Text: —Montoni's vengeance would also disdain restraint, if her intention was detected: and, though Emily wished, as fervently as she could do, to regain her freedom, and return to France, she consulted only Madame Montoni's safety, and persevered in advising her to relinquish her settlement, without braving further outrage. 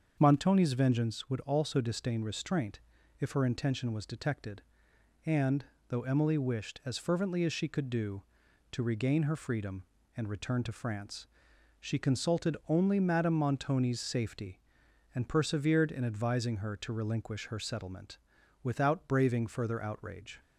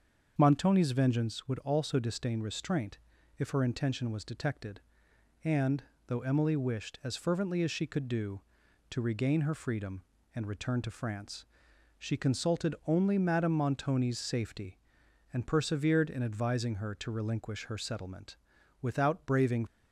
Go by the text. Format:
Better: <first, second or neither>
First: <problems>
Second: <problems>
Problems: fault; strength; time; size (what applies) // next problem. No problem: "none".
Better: first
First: starts louder than the rest; until 1.2 s; 6.5 dB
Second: starts louder than the rest; until 1.3 s; 6.5 dB // stops before "further outrage"; at 19.6 s